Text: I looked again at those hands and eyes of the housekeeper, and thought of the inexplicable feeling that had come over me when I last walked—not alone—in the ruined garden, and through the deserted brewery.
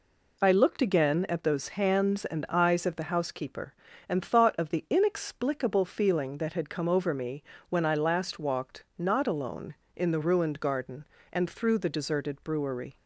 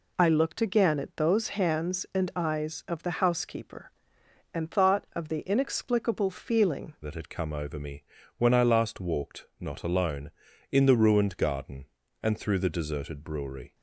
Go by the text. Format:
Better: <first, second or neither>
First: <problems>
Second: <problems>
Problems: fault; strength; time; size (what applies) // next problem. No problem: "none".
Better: first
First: pauses between "me" and "when"; slight; at 7.4 s; 0.28 s long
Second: changes voice at "that"; from 7.0 s on; 6.7 s long // pauses between "me" and "when"; slight; at 8.0 s; 0.34 s long